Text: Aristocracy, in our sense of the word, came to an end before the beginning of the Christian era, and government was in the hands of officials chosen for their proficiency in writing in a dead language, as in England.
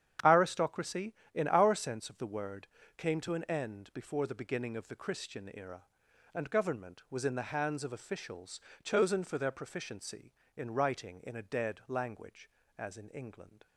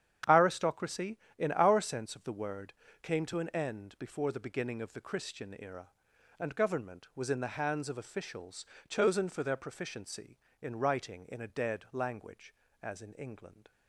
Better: neither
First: starts louder than the rest; strong; until 1.4 s; 9.5 dB // pauses between "officials" and "chosen"; slight; at 8.5 s; 0.24 s long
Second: starts louder than the rest; strong; until 1.4 s; 9.5 dB // pauses between "officials" and "chosen"; slight; at 8.6 s; 0.24 s long

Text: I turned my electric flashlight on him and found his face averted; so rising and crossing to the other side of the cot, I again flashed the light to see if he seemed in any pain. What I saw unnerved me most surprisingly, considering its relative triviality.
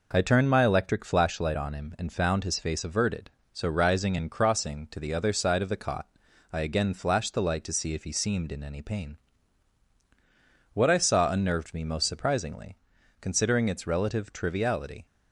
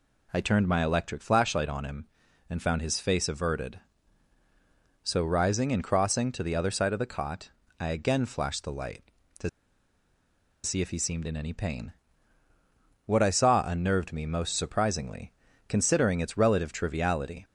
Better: first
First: none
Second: pauses between "to" and "see"; at 9.4 s; 1.1 s long

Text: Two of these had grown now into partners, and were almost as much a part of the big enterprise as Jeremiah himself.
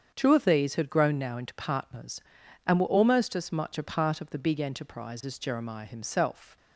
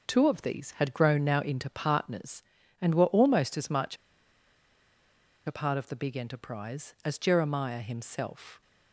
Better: first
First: starts louder than the rest; strong; until 1.1 s; 7.5 dB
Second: starts louder than the rest; noticeable; until 1.1 s; 6 dB // pauses between "much" and "a"; strong; at 3.9 s; 1.5 s long

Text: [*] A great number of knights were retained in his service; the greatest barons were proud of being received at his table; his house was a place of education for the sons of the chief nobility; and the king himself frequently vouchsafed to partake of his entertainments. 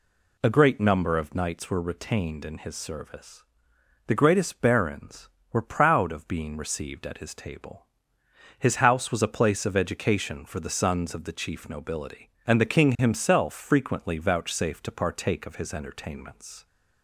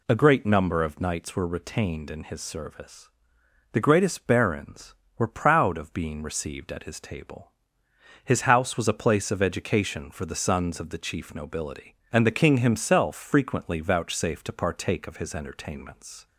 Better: neither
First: none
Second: none

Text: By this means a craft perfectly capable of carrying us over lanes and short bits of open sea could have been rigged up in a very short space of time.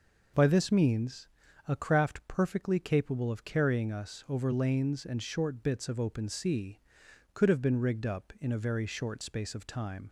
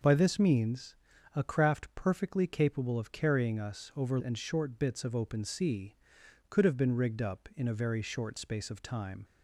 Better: first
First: pauses between "means" and "a"; at 1.2 s; 0.40 s long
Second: pauses between "means" and "a"; at 0.9 s; 0.40 s long // skips "lanes"; at 4.1 s

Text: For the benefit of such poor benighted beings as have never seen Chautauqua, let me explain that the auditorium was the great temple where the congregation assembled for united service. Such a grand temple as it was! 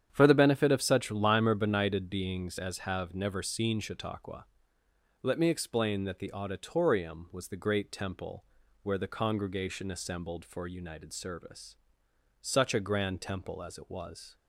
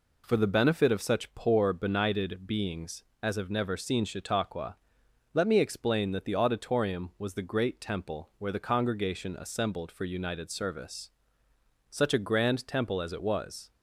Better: second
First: starts louder than the rest; strong; until 1.1 s; 9 dB // says "limer" for "poor"; at 1.0 s // pauses between "temple" and "where"; at 8.4 s; 0.38 s long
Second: none

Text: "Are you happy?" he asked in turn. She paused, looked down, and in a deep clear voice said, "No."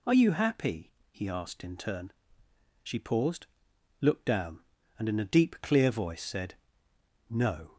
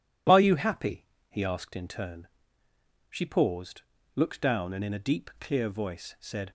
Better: first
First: none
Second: stops before "No"; at 6.4 s

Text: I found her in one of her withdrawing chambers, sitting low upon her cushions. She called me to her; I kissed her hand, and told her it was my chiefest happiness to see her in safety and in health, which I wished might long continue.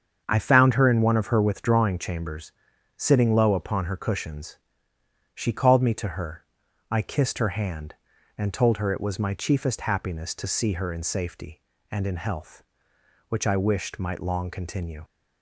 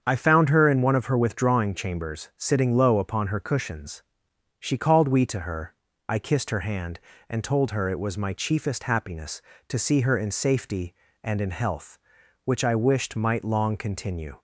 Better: first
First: starts louder than the rest; strong; until 1.2 s; 7.5 dB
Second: starts louder than the rest; strong; until 1.0 s; 7.5 dB // says "we" for "me"; at 5.0 s

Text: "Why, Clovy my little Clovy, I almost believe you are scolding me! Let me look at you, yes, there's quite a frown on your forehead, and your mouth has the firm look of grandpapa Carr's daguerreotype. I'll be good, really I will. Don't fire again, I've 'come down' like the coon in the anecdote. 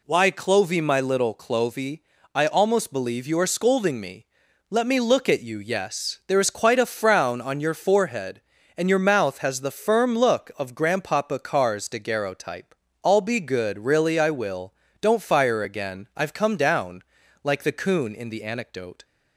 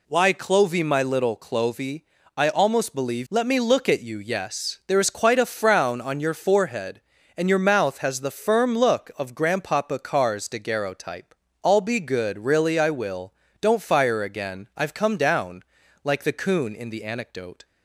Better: first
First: pauses between "down" and "like"; at 17.0 s; 0.42 s long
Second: skips "you are scolding me"; at 3.2 s // pauses between "down" and "like"; at 15.6 s; 0.42 s long

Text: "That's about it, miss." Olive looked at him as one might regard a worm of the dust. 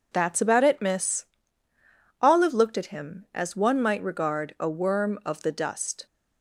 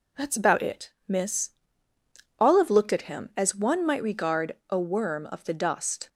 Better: neither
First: none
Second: none

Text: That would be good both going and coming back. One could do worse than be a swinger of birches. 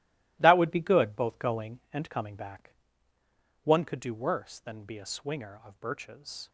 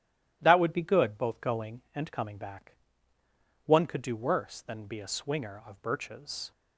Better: second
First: gets quieter; strong; throughout; 11 dB // starts louder than the rest; strong; until 1.4 s; 17 dB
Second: starts louder than the rest; strong; until 1.4 s; 13 dB

